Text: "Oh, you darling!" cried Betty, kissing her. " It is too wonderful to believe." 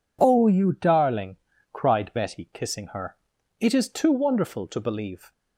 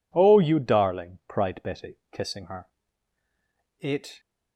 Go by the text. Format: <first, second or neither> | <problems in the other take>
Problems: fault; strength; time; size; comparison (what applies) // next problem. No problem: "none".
first | stops before "is too wonderful to believe"; at 4.1 s